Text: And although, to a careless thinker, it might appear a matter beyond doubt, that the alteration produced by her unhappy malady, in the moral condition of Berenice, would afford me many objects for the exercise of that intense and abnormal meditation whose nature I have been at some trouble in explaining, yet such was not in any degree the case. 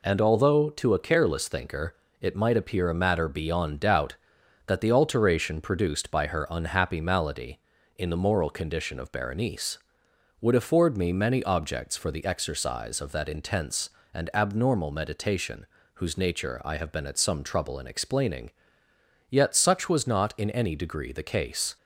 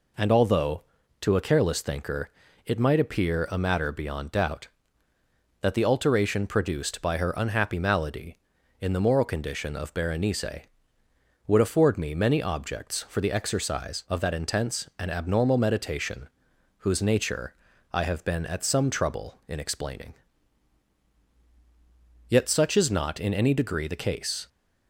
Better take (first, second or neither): first